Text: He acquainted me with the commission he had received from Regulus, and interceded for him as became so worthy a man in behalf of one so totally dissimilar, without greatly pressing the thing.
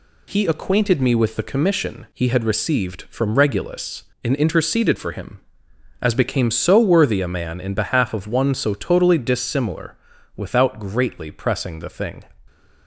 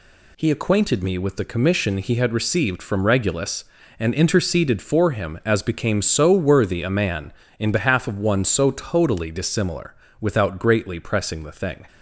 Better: neither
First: none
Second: none

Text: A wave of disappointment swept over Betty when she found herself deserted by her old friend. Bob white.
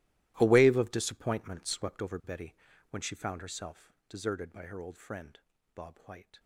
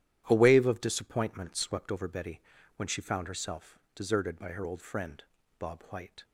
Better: second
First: gets quieter; strong; throughout; 19 dB // pauses between "Betty" and "when"; at 2.5 s; 0.38 s long // pauses between "herself" and "deserted"; slight; at 3.9 s; 0.16 s long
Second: pauses between "Betty" and "when"; at 2.3 s; 0.38 s long // pauses between "herself" and "deserted"; slight; at 3.7 s; 0.16 s long

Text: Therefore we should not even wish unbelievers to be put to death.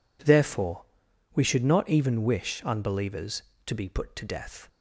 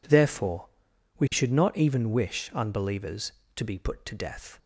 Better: neither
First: pauses between "Therefore" and "we"; noticeable; at 0.8 s; 0.50 s long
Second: pauses between "Therefore" and "we"; noticeable; at 0.6 s; 0.50 s long

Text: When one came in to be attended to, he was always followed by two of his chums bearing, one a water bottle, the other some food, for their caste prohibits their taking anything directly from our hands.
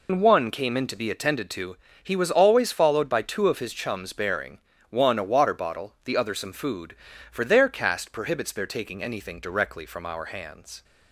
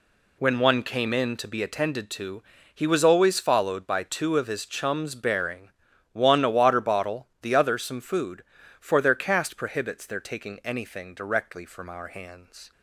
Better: second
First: loses the start of "When"; at 0.0 s; 100 ms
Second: none

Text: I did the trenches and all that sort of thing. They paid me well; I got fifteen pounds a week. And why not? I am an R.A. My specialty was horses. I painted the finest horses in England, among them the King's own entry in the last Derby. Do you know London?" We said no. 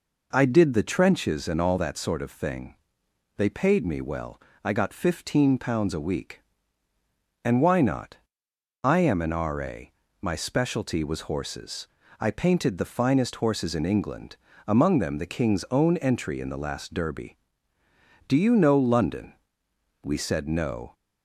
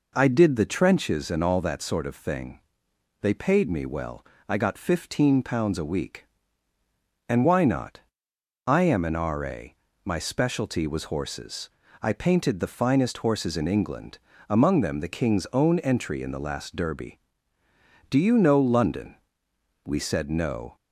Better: neither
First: none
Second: none

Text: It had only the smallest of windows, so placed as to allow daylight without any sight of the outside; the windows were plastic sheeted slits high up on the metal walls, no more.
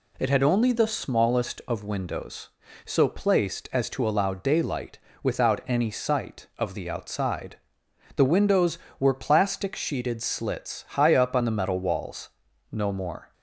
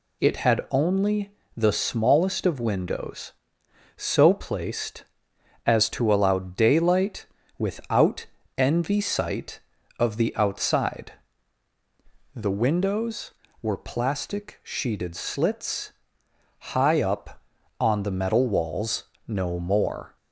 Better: first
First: pauses between "daylight" and "without"; slight; at 4.9 s; 0.26 s long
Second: pauses between "only" and "the"; slight; at 1.3 s; 0.24 s long // pauses between "daylight" and "without"; slight; at 7.2 s; 0.32 s long // says "envy" for "any"; at 8.5 s // pauses between "slits" and "high"; noticeable; at 15.9 s; 0.82 s long

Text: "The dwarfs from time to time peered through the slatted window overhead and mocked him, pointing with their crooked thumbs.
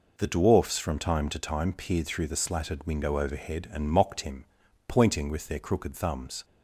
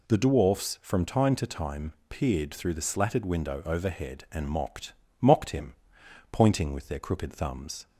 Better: first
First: none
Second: pauses between "time" and "peered"; slight; at 1.9 s; 0.16 s long // says "mocked" twice; at 5.1 s

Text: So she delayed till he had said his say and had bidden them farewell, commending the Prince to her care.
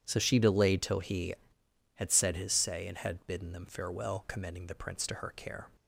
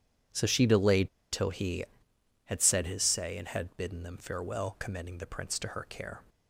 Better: first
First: none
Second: starts louder than the rest; strong; until 1.5 s; 9.5 dB // pauses between "delayed" and "till"; slight; at 1.0 s; 0.23 s long

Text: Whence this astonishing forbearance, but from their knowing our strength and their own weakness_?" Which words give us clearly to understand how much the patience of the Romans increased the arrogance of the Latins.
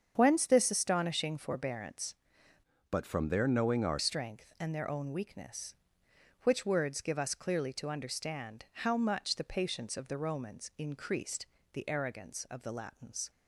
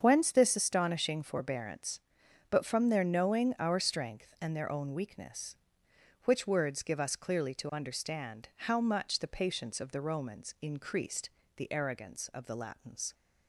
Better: second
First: starts louder than the rest; strong; until 1.1 s; 7.5 dB // changes voice from "but" to "our"; from 2.8 to 3.9 s; 1.1 s long // pauses between "increased" and "the"; slight; at 11.4 s; 0.26 s long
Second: starts louder than the rest; strong; until 1.0 s; 7 dB // pauses between "increased" and "the"; slight; at 11.2 s; 0.26 s long

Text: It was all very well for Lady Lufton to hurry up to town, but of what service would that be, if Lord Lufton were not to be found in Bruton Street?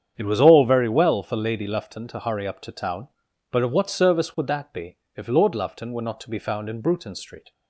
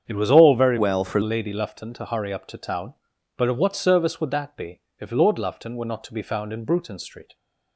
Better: first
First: starts louder than the rest; strong; until 1.1 s; 8 dB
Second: starts louder than the rest; strong; until 1.0 s; 8 dB // changes voice from "well" to "for"; from 0.7 to 1.2 s; 0.5 s long

